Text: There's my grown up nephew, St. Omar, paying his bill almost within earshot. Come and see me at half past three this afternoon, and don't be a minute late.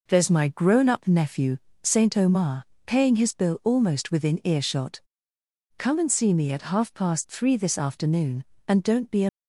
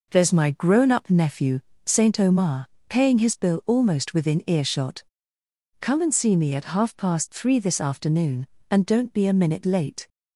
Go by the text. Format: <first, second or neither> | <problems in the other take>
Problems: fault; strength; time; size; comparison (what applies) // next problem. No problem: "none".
second | stops before "minute late"; at 9.2 s